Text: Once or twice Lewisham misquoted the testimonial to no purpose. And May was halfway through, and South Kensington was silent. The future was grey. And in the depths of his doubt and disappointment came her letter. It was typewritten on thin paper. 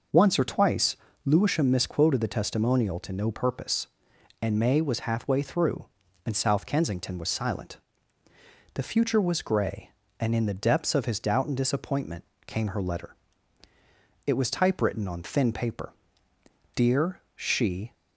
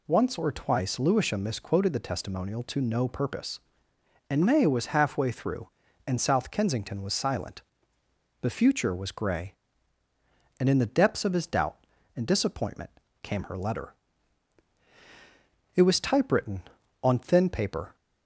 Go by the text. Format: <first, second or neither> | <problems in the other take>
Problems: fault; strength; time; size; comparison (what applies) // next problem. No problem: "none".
second | pauses between "twice" and "Lewisham"; slight; at 0.9 s; 0.28 s long // pauses between "disappointment" and "came"; slight; at 12.2 s; 0.22 s long; slight in the second // goes on to say "Dear she"; noticeable; from 16.7 s on; 1.1 s long